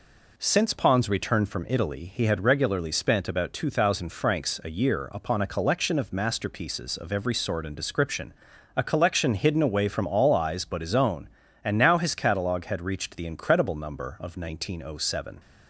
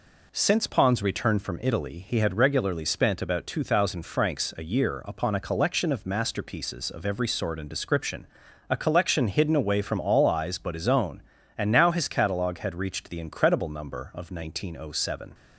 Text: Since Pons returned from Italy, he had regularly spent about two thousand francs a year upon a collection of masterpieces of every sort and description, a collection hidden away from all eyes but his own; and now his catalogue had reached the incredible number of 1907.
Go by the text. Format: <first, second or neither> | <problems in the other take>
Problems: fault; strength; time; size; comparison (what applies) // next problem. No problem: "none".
neither | none